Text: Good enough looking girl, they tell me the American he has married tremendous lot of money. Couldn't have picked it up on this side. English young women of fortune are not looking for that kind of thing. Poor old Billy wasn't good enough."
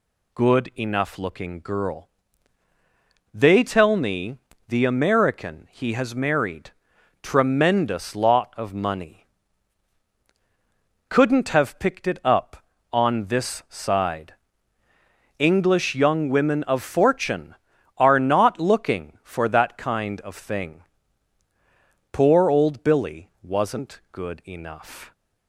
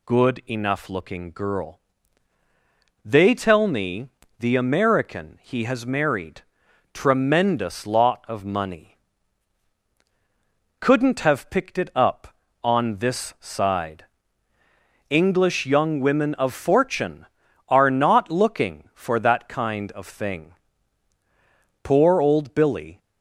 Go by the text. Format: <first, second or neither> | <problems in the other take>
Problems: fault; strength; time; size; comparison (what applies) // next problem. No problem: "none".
first | pauses between "me" and "the"; slight; at 4.0 s; 0.32 s long; slight in the first // pauses between "married" and "tremendous"; noticeable; at 6.4 s; 0.52 s long; noticeable in the first // stops before "wasn't good enough"; at 22.9 s